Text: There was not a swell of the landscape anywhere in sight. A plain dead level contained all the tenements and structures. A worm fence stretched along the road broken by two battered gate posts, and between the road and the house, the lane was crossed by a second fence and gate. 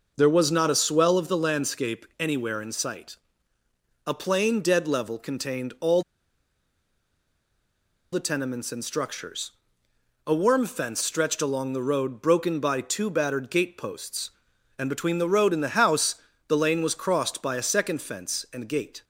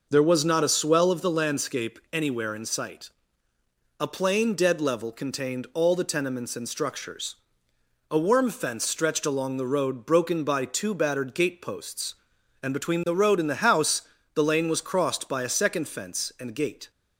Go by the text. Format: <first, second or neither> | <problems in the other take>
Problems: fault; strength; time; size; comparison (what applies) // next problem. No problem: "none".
second | pauses between "all" and "the"; strong; at 6.0 s; 2.1 s long